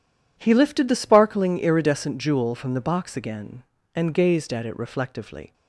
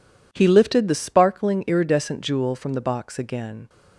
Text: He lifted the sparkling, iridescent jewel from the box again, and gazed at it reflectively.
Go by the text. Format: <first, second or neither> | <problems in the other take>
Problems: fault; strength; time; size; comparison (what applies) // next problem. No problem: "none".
first | stops before "and gazed at it reflectively"; at 3.6 s